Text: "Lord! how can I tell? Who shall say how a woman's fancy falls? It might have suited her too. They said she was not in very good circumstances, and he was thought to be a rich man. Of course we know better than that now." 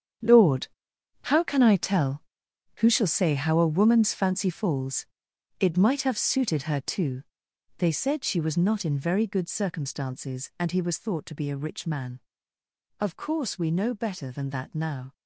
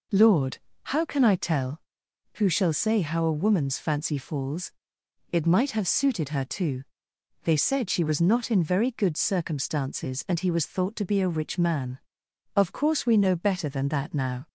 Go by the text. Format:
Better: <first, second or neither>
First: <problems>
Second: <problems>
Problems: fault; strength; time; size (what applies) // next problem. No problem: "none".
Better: second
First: gets quieter; strong; throughout; 12.5 dB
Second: none